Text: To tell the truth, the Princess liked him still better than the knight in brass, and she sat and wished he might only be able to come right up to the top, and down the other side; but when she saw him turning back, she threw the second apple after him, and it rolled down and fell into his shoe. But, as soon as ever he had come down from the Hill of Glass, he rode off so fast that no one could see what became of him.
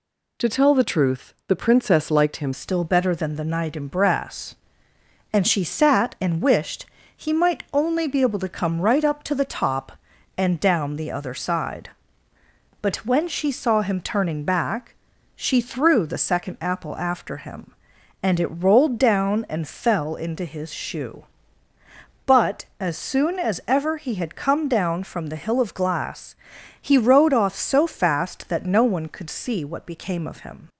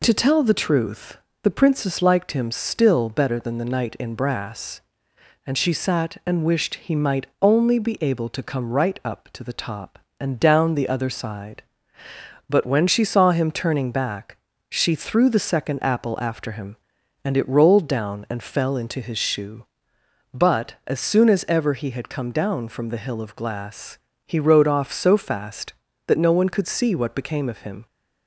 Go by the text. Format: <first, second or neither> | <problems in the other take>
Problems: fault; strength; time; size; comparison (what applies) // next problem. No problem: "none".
second | changes voice at "still"; from 2.5 s on; 28.1 s long // pauses between "wished" and "he"; slight; at 6.8 s; 0.32 s long